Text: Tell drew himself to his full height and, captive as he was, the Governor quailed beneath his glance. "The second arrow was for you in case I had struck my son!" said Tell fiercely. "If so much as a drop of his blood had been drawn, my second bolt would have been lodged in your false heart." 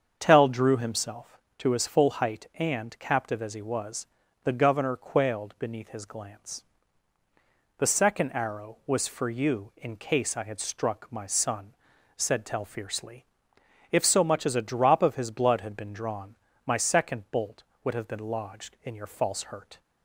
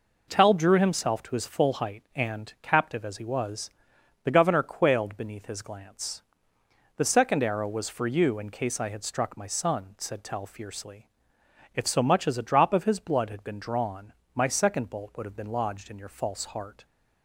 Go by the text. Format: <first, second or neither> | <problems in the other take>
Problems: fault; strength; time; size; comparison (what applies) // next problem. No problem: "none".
second | starts louder than the rest; strong; until 1.1 s; 7 dB // says "hurt" for "heart"; at 19.4 s